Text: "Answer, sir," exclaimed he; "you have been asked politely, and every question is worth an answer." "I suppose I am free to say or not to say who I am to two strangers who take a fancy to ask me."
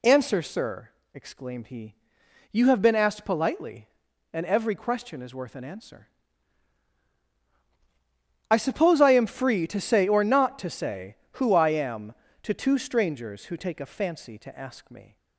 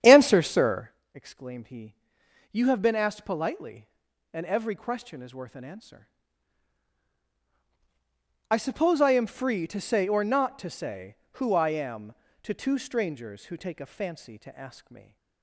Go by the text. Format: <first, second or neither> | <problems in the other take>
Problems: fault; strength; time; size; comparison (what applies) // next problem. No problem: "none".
first | starts louder than the rest; strong; until 1.0 s; 9 dB